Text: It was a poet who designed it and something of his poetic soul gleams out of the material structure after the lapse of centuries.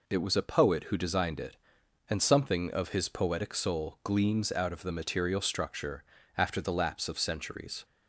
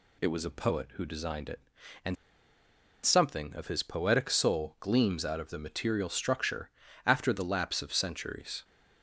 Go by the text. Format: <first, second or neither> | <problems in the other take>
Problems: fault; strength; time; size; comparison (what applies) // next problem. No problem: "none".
first | pauses between "and" and "something"; noticeable; at 2.1 s; 0.90 s long // pauses between "structure" and "after"; slight; at 6.7 s; 0.36 s long; slight in the first